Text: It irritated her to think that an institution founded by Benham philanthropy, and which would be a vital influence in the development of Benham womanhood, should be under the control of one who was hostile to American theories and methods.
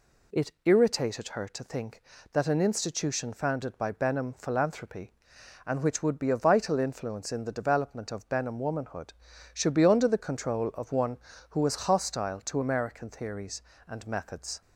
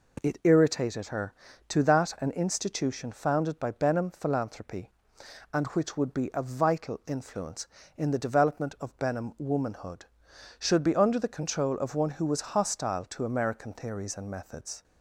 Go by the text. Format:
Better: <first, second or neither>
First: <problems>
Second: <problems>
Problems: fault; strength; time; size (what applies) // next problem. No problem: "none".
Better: first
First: none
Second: skips "think"; at 1.8 s